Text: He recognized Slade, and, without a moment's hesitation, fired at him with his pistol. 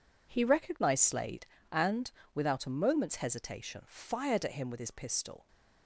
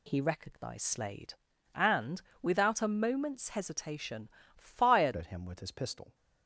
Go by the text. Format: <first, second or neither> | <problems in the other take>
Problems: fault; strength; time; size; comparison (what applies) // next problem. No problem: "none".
first | changes voice at "at"; from 5.1 s on; 1.0 s long